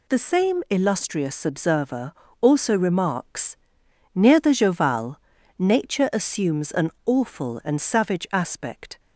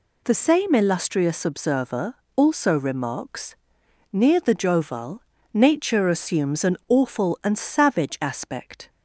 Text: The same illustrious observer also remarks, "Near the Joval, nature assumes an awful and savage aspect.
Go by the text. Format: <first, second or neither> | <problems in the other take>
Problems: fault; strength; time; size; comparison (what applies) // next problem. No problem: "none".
neither | pauses between "observer" and "also"; slight; the same in both